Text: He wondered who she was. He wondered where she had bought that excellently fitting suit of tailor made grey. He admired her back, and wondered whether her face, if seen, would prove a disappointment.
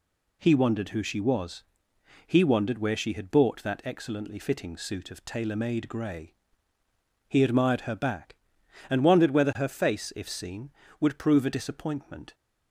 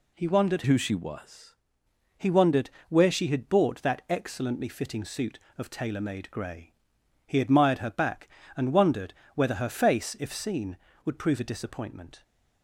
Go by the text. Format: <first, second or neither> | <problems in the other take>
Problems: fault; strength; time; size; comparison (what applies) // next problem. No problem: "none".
first | changes voice from "who" to "was"; from 0.6 to 1.5 s; 0.9 s long // pauses between "wondered" and "where"; slight; at 2.7 s; 0.18 s long // pauses between "wondered" and "whether"; slight; at 9.1 s; 0.22 s long